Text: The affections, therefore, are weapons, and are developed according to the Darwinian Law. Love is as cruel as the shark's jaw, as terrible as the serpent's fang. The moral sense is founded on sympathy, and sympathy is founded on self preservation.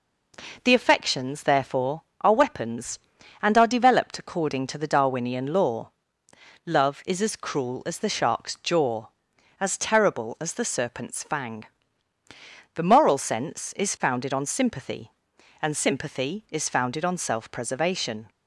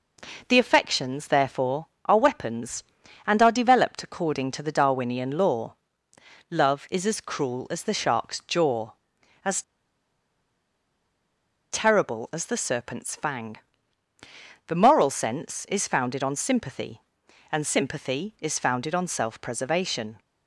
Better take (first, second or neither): first